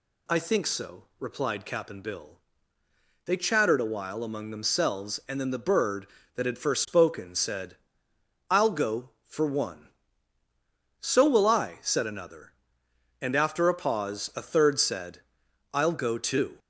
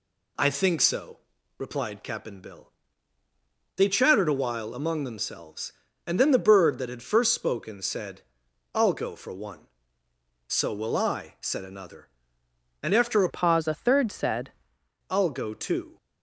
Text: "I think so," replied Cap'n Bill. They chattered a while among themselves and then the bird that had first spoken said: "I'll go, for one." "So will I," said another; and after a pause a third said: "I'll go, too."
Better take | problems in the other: first | changes voice from "pause" to "said"; from 13.2 to 14.5 s; 1.3 s long

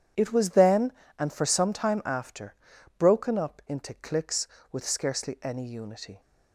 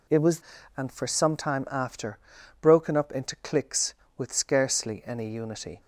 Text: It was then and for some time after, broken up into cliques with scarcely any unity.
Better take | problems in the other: first | skips "then"; at 0.5 s

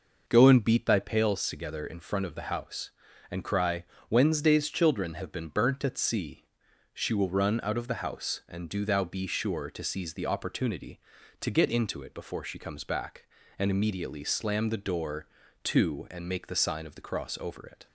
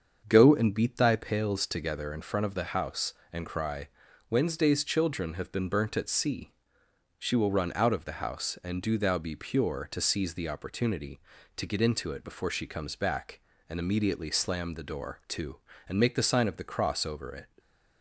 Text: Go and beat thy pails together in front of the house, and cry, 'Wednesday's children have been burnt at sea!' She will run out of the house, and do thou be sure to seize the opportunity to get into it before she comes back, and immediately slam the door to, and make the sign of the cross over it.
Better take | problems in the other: first | starts louder than the rest; until 1.2 s; 7 dB // says "pure" for "sure"; at 9.3 s

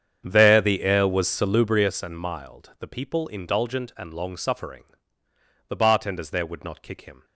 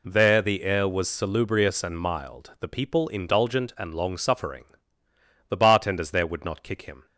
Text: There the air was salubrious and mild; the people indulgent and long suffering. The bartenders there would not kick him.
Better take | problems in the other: second | starts louder than the rest; strong; until 2.0 s; 8 dB

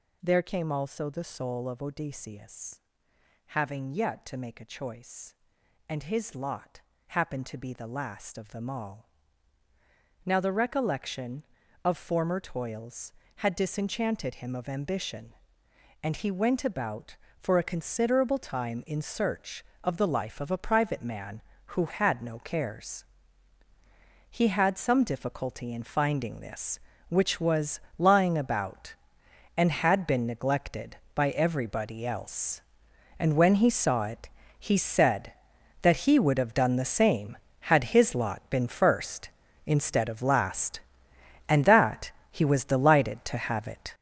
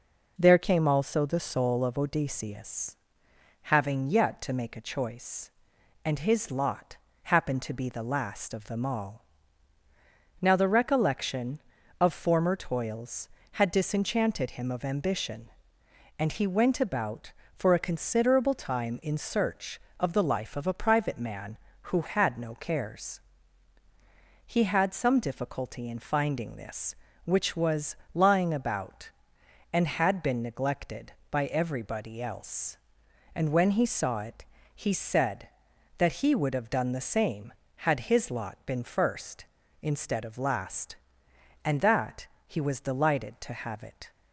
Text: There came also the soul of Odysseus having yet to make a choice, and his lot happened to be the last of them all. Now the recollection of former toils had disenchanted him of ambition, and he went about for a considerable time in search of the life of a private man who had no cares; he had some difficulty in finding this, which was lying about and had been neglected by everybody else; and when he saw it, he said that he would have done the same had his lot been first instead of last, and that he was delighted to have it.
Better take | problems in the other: second | gets louder; strong; throughout; 9 dB // pauses between "Odysseus" and "having"; noticeable; at 2.8 s; 0.74 s long; noticeable in the second // pauses between "lot" and "happened"; slight; at 6.8 s; 0.26 s long; slight in the second // pauses between "was" and "lying"; slight; at 27.8 s; 0.18 s long; slight in the second // pauses between "that" and "he"; slight; at 42.1 s; 0.20 s long; slight in the second

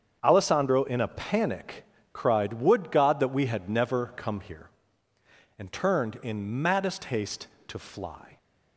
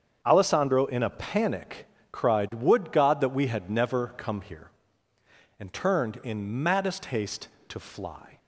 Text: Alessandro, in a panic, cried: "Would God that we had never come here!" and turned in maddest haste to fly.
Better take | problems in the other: neither | starts louder than the rest; strong; the same in both

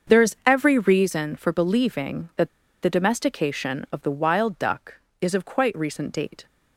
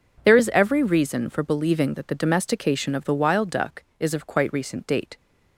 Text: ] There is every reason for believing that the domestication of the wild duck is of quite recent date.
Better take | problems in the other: second | starts louder than the rest; until 1.1 s; 6.5 dB // pauses between "that" and "the"; slight; at 2.4 s; 0.34 s long

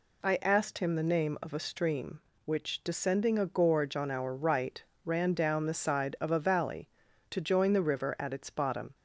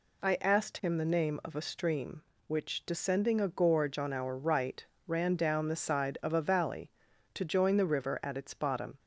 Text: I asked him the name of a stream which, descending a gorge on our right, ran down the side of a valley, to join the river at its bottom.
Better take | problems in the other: neither | none

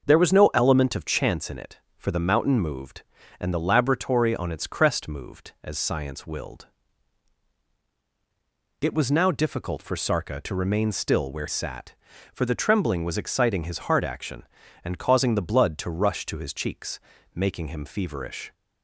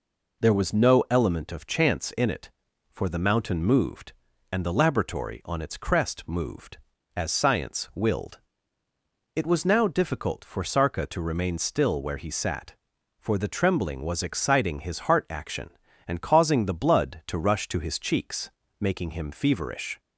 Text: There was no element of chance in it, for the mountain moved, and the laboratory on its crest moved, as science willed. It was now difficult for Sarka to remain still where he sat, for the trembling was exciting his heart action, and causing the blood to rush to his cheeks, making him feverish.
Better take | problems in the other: second | starts louder than the rest; noticeable; until 1.1 s; 6 dB // skips "he"; at 11.4 s

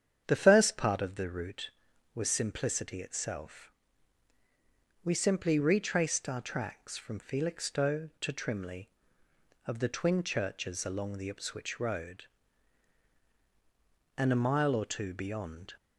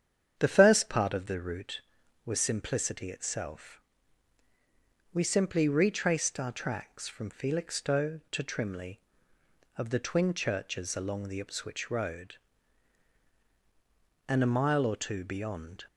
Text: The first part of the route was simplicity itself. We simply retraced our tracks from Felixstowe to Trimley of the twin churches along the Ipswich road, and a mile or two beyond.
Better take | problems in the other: neither | starts louder than the rest; strong; the same in both

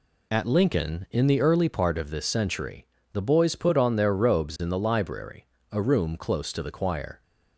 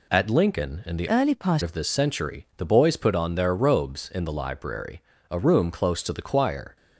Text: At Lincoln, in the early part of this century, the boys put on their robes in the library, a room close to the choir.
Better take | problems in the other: first | changes voice from "early" to "part"; from 1.0 to 1.6 s; 0.6 s long

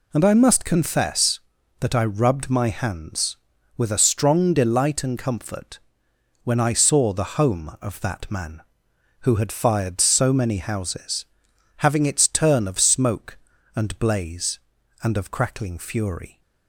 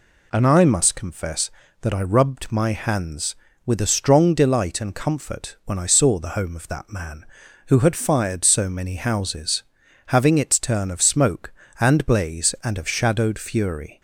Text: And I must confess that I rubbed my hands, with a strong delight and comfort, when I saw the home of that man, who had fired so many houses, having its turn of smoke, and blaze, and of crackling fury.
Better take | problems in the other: first | says "shadowed" for "crackling"; at 12.8 s

